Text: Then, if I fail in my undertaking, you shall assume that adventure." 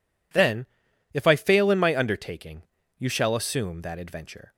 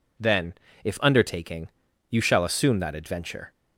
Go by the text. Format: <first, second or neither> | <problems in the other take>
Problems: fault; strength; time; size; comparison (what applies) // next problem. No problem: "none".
first | skips "I fail in my"; at 1.0 s